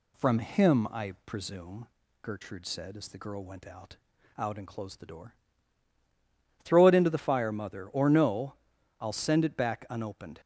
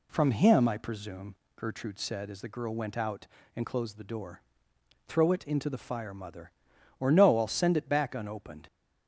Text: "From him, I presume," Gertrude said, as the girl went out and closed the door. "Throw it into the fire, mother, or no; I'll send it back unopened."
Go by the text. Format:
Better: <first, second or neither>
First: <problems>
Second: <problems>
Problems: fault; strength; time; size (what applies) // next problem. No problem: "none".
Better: second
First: says "out" twice; at 4.3 s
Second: none